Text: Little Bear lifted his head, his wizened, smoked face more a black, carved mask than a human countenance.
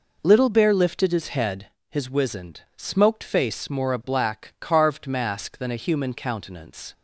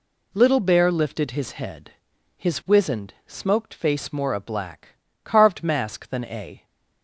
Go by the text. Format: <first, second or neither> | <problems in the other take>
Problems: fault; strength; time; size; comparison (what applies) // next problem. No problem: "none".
first | stops before "human countenance"; at 6.6 s